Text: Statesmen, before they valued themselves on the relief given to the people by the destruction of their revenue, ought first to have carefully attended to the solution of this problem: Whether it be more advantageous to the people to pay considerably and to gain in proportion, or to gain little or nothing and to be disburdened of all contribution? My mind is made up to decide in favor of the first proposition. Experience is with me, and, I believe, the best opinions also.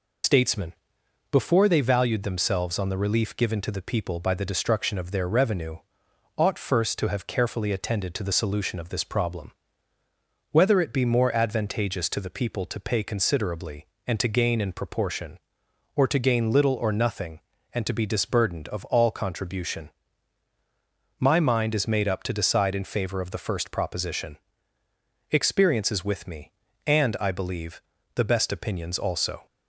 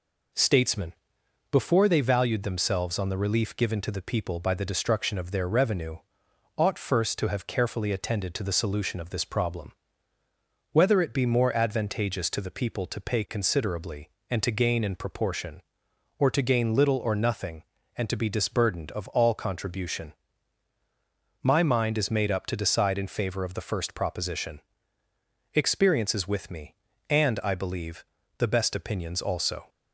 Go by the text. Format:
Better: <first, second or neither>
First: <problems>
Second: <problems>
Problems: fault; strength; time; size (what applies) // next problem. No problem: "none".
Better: second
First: loses the start of "Statesmen"; at 0.2 s; 100 ms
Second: none